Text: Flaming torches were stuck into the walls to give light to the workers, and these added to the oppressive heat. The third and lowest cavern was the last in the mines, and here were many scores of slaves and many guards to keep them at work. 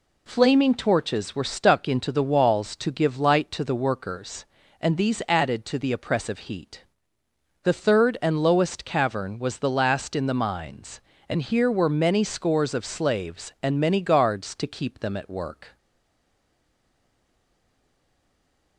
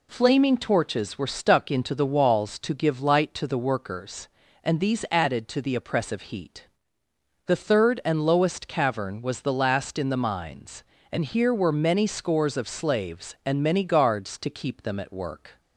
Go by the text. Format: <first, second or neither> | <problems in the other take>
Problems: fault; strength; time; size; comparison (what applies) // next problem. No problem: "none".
second | stays silent after the last word; strong; from 15.7 s on; 3.0 s long